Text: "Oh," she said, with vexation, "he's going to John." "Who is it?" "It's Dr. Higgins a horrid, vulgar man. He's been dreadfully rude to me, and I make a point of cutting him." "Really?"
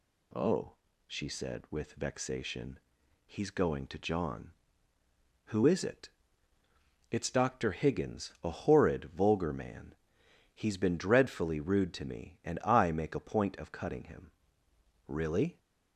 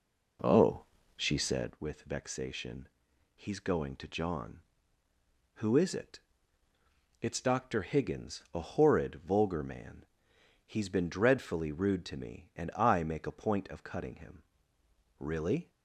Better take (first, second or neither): first